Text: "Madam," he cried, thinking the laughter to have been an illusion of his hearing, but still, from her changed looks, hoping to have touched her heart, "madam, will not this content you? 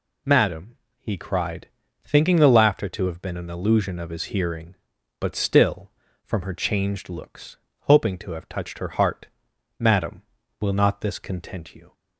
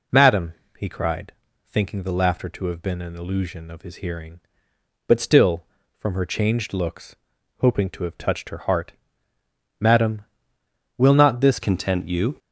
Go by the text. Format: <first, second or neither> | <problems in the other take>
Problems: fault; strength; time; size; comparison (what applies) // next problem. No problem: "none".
first | changes voice at "content"; from 11.6 s on; 0.7 s long